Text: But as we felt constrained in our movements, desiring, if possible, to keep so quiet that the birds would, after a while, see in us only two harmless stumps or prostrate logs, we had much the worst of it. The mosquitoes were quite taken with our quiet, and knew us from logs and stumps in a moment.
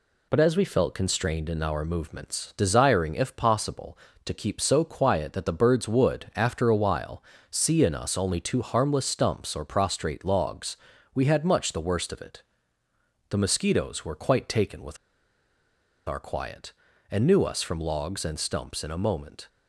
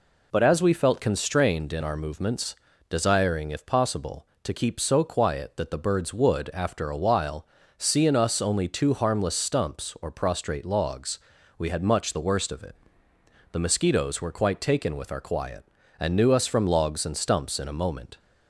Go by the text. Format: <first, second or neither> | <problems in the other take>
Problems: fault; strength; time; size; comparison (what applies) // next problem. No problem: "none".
second | pauses between "with" and "our"; at 14.9 s; 1.1 s long